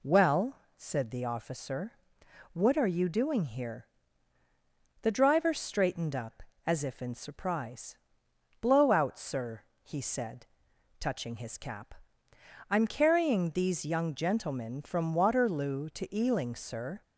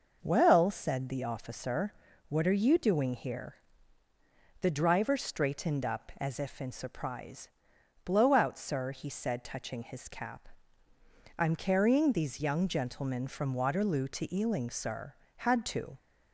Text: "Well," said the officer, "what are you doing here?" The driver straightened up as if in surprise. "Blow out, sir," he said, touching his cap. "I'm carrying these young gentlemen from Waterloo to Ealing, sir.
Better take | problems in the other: first | goes on to say "Had to"; from 15.3 s on; 0.60 s long

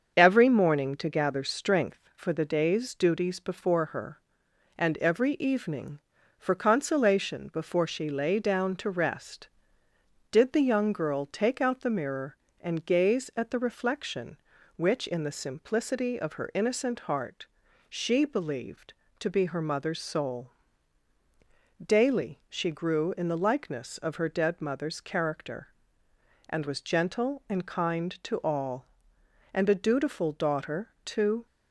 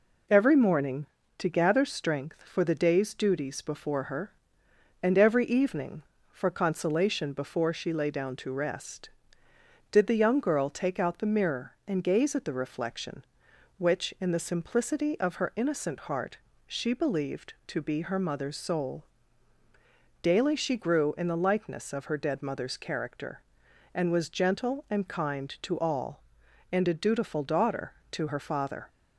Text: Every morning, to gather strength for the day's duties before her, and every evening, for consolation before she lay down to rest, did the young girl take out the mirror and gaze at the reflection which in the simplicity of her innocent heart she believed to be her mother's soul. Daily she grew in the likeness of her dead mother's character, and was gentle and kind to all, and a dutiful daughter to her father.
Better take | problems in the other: second | starts louder than the rest; strong; until 1.2 s; 7 dB // pauses between "heart" and "she"; at 17.4 s; 0.42 s long; slight in the second // stops before "her father"; at 31.4 s

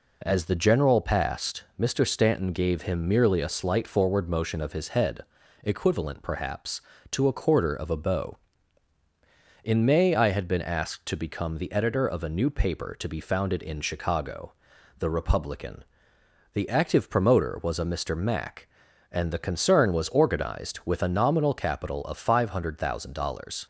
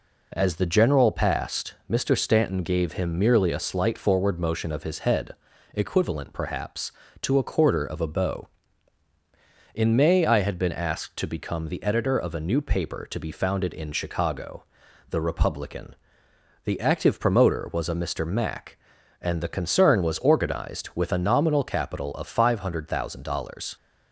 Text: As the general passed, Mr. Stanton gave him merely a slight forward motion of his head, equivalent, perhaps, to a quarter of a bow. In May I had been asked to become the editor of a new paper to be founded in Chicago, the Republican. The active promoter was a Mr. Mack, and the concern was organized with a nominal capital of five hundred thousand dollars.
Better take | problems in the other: neither | none

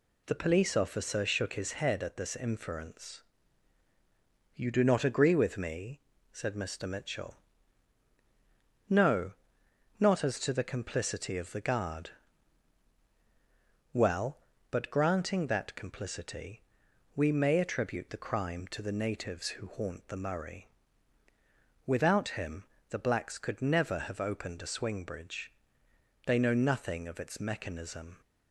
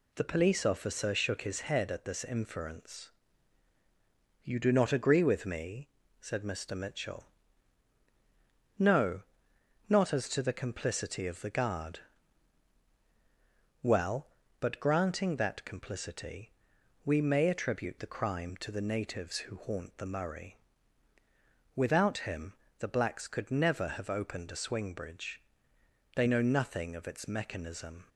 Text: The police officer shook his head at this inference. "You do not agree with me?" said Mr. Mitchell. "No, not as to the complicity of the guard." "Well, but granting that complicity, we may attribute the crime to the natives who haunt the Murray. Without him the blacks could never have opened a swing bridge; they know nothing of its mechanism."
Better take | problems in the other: neither | pauses between "him" and "the"; slight; the same in both

